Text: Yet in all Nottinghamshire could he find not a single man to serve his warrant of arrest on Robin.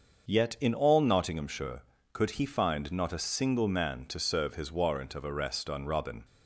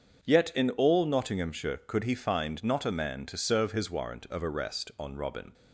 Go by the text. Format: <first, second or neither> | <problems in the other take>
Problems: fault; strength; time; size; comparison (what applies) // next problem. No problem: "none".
first | starts louder than the rest; until 1.3 s; 7 dB; also in the first // skips "single"; at 2.9 s